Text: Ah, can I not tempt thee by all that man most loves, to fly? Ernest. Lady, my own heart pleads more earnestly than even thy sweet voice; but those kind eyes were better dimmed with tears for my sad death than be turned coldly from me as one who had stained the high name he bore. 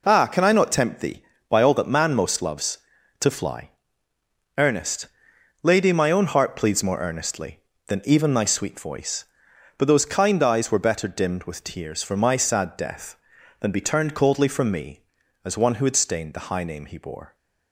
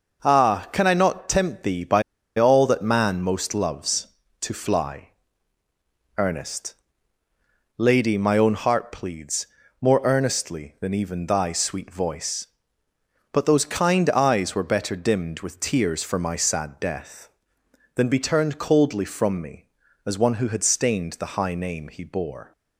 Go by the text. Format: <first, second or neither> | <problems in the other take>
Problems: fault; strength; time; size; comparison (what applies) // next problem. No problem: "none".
first | pauses between "by" and "all"; slight; at 2.0 s; 0.35 s long // pauses between "pleads" and "more"; slight; at 9.4 s; 0.34 s long